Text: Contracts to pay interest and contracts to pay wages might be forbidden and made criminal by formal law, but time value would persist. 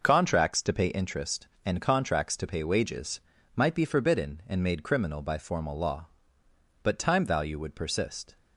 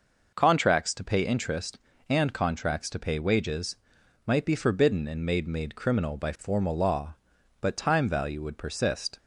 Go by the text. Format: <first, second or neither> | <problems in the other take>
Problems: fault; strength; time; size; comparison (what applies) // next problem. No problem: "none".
first | pauses between "wages" and "might"; noticeable; at 3.7 s; 0.48 s long; slight in the first // says "made" twice; at 5.4 s